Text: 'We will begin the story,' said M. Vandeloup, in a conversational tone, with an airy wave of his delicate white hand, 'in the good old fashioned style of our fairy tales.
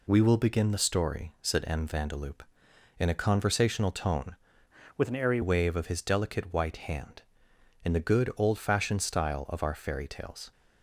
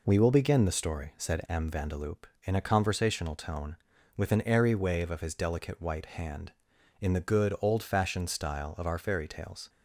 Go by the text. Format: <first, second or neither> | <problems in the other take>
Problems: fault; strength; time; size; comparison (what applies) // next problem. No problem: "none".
second | changes voice from "with" to "airy"; from 4.9 to 5.3 s; 0.4 s long